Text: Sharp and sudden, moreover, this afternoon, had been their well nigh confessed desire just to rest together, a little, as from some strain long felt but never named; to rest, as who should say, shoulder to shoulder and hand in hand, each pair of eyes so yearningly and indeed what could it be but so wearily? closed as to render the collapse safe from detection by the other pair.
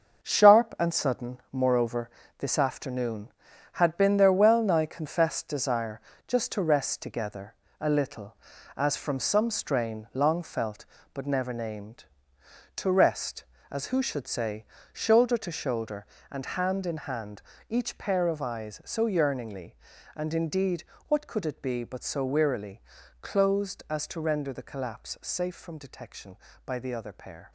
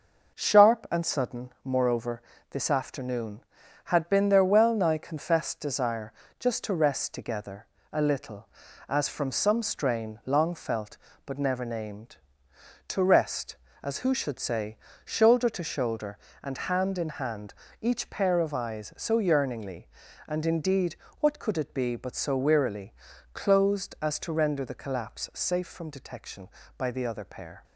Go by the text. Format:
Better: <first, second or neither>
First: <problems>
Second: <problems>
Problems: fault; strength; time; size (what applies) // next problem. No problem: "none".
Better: second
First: gets quieter; strong; throughout; 8 dB // pauses between "desire" and "just"; slight; at 6.0 s; 0.26 s long // pauses between "indeed" and "what"; slight; at 20.8 s; 0.24 s long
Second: pauses between "desire" and "just"; slight; at 6.1 s; 0.26 s long // pauses between "indeed" and "what"; slight; at 20.9 s; 0.24 s long